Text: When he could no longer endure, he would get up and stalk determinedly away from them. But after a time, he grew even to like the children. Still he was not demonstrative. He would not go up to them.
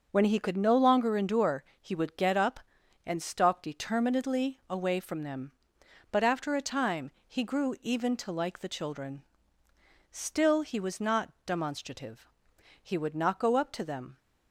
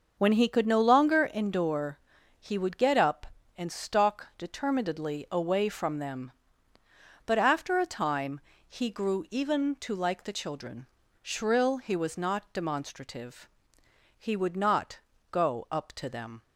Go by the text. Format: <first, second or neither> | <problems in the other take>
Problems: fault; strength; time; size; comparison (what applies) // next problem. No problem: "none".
first | says "Shrill" for "Still"; at 11.2 s // pauses between "not" and "go"; slight; at 14.9 s; 0.32 s long